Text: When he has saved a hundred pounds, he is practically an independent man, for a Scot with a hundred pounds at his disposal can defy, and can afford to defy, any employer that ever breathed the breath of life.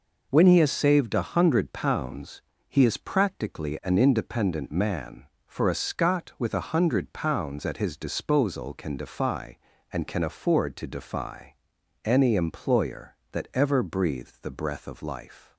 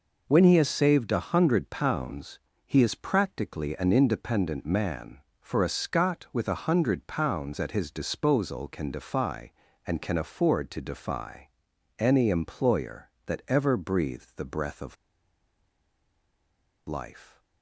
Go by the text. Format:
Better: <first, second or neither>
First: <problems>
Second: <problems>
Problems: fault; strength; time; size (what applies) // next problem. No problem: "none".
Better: first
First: none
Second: pauses between "of" and "life"; strong; at 14.9 s; 1.9 s long